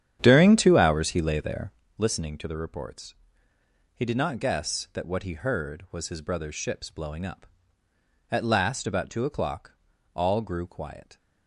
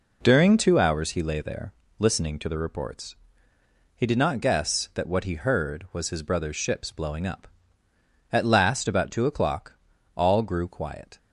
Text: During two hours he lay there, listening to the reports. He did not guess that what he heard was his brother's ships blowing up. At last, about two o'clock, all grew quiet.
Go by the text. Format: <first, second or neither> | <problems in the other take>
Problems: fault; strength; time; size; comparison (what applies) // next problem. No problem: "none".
second | starts louder than the rest; strong; until 1.9 s; 9.5 dB